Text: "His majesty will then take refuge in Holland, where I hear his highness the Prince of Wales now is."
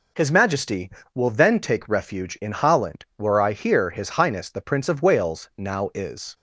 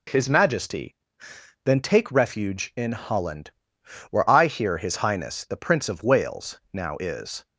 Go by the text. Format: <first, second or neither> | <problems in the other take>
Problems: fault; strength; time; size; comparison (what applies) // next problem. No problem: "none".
first | skips "will"; at 1.3 s